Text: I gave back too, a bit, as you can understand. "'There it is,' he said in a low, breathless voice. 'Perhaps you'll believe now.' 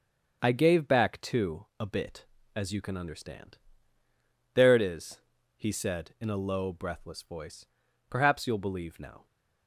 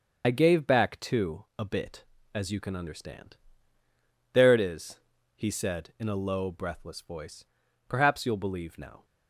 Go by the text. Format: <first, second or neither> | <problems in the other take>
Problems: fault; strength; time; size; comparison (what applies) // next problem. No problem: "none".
first | loses the start of "I"; at 0.2 s; 45 ms // starts louder than the rest; until 1.2 s; 6.5 dB; also in the first